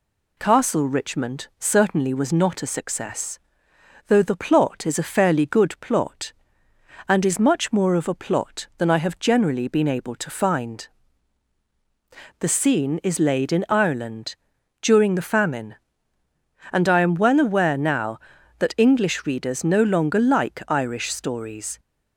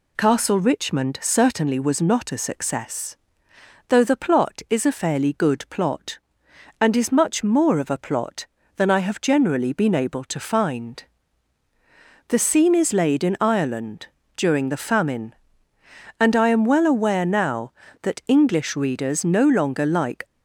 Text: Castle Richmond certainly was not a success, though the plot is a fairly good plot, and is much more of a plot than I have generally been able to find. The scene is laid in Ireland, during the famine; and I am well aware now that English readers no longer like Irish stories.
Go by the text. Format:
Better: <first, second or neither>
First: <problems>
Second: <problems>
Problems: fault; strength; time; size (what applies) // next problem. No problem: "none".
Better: first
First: none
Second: stops before "Irish stories"; at 20.2 s